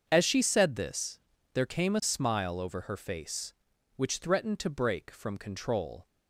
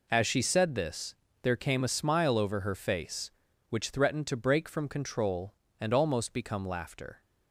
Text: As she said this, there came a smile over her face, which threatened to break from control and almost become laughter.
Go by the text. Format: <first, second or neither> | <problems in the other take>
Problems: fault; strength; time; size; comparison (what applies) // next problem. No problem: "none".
second | starts louder than the rest; until 1.0 s; 7 dB // stops before "and almost become laughter"; at 6.0 s